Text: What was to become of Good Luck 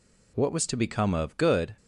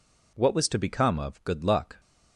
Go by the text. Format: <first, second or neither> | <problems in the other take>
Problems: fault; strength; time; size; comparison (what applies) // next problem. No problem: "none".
second | stops before "Luck"; at 1.7 s